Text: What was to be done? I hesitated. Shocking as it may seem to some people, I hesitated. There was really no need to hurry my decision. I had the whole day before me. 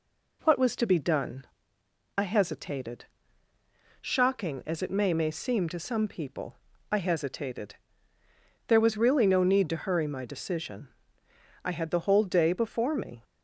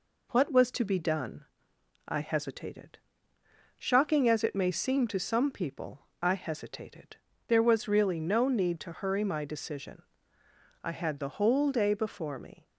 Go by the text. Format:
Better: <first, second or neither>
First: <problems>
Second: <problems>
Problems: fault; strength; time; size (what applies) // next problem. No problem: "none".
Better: second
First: says "may" twice; at 5.1 s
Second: none